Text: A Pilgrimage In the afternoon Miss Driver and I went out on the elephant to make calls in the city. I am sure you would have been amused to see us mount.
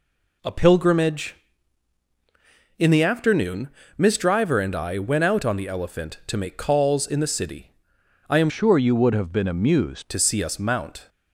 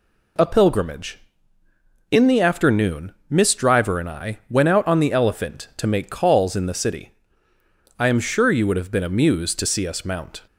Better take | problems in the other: second | pauses between "afternoon" and "Miss"; slight; at 3.6 s; 0.30 s long // changes voice from "sure" to "amused"; from 8.4 to 10.0 s; 1.6 s long

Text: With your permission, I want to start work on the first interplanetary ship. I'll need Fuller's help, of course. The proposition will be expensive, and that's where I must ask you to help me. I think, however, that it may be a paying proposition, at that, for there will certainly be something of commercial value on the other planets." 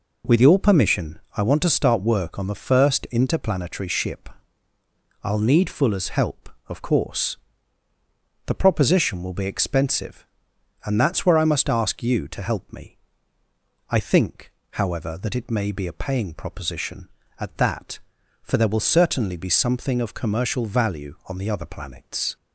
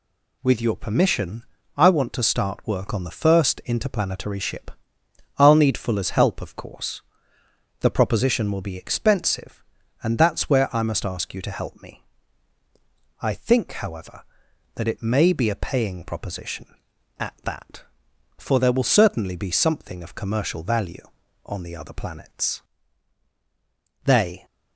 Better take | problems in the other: first | goes on to say "They"; slight; from 24.0 s on; 0.40 s long

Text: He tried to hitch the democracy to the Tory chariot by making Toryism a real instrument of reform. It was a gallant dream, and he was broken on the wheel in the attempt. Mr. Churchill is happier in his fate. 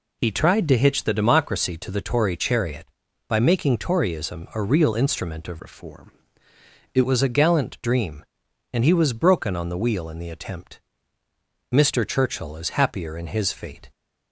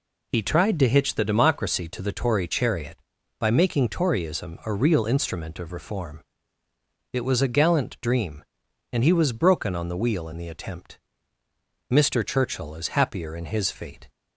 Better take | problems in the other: second | changes voice from "reform" to "It"; from 5.5 to 7.0 s; 1.5 s long

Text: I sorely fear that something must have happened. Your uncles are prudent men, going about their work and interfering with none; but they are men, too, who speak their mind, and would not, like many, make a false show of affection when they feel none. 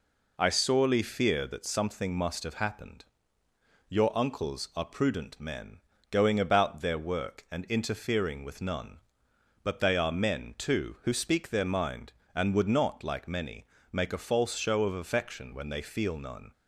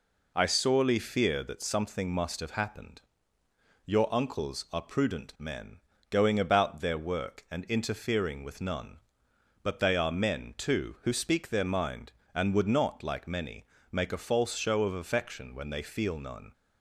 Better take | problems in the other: neither | none

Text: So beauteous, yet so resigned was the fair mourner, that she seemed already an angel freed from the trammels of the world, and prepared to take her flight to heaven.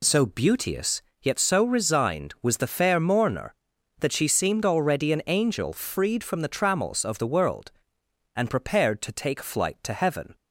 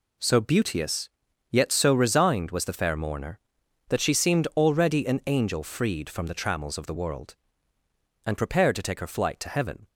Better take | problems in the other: second | skips "her"; at 9.4 s

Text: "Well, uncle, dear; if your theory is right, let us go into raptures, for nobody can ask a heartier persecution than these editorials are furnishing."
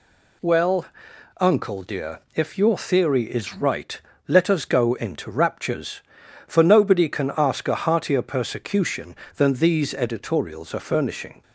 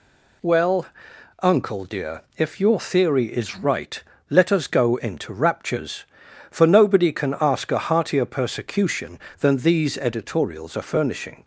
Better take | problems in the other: neither | none

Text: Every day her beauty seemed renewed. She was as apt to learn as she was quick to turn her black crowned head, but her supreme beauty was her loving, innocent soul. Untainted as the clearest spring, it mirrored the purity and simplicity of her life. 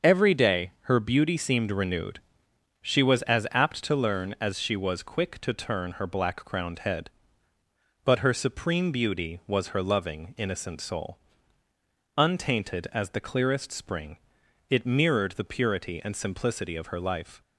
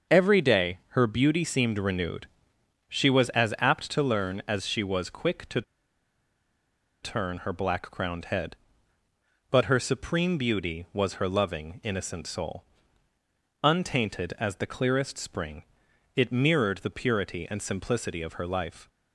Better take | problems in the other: first | starts louder than the rest; until 1.2 s; 6.5 dB; also in the first // pauses between "to" and "turn"; strong; at 5.6 s; 1.4 s long

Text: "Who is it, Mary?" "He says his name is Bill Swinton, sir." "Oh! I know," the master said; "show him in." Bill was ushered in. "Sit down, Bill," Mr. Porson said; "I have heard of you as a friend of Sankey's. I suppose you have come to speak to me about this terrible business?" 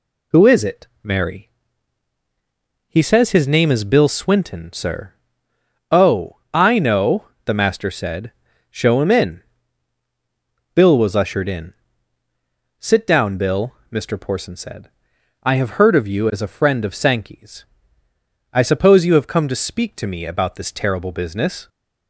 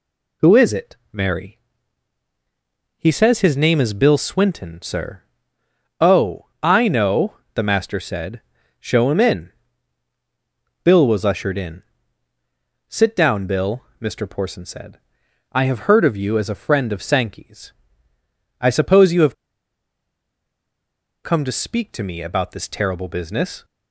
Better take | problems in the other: first | pauses between "have" and "come"; strong; at 19.3 s; 1.8 s long

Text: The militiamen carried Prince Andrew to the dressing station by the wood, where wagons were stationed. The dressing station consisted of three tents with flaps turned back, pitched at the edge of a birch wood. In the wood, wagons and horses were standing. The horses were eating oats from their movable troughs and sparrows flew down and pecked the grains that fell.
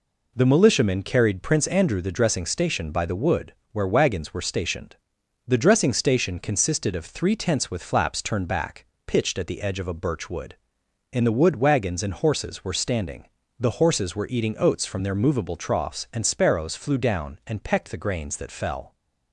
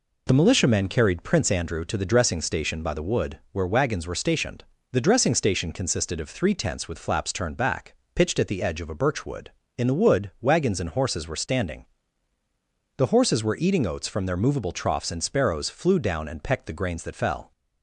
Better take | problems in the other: second | skips "to"; at 2.0 s

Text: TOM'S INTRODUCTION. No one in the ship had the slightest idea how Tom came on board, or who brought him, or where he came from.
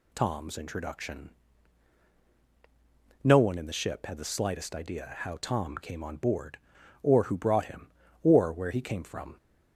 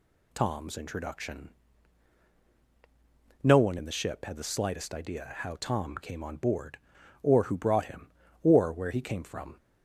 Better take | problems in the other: neither | none

